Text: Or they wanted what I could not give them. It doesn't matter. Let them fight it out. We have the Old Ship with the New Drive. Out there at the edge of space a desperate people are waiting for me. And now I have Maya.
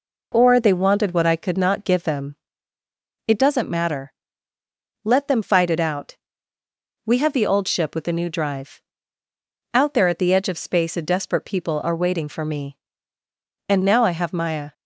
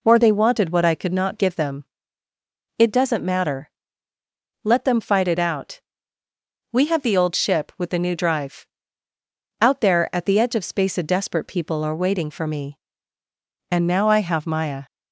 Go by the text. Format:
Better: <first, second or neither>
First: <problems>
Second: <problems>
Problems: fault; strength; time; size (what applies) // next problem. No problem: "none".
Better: neither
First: none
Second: none